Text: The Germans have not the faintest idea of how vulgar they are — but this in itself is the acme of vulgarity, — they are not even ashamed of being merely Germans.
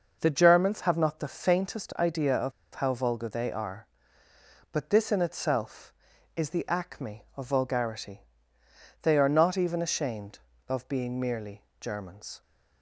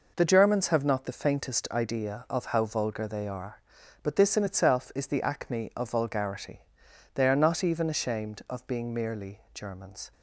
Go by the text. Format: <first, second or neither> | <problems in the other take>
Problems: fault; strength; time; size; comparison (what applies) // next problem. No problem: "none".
second | pauses between "of" and "how"; slight; at 2.5 s; 0.23 s long // pauses between "merely" and "Germans"; slight; at 11.6 s; 0.18 s long